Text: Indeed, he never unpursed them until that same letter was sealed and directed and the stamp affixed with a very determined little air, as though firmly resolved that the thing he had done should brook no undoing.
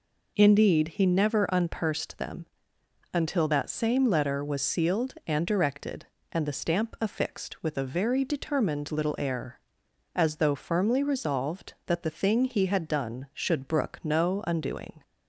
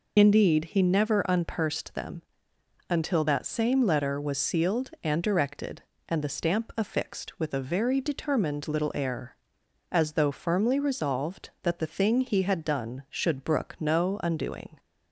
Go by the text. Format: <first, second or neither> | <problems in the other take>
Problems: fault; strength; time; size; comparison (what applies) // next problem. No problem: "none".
first | loses the start of "Indeed"; at 0.1 s; 40 ms // pauses between "them" and "until"; noticeable; at 2.2 s; 0.66 s long; noticeable in the first